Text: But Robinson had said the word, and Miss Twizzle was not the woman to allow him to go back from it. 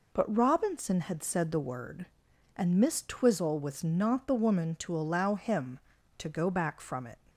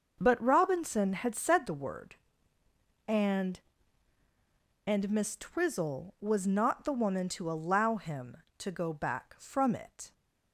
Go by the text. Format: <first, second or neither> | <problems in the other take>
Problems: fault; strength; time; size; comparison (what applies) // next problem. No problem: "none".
first | starts louder than the rest; noticeable; until 1.1 s; 6 dB // says "and" twice; at 4.8 s